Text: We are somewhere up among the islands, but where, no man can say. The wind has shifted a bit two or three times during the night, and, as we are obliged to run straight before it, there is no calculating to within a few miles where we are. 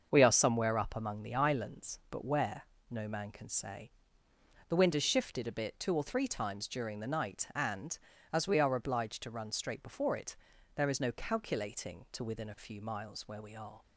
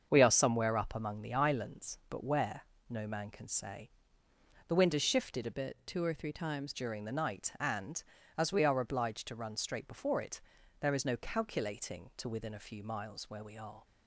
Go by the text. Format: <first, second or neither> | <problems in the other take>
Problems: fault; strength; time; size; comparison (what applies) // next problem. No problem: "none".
first | starts louder than the rest; until 1.1 s; 7 dB; also in the first // changes voice from "bit" to "times"; from 5.5 to 6.7 s; 1.2 s long